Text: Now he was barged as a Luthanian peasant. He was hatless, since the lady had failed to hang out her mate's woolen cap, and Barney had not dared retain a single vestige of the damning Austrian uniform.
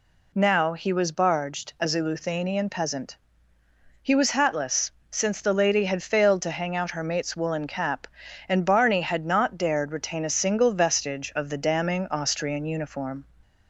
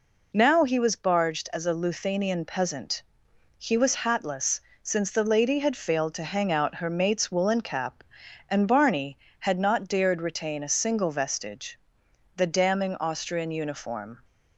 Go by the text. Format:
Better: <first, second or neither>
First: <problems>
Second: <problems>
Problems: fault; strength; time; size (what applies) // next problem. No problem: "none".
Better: first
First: none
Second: skips "of"; at 12.0 s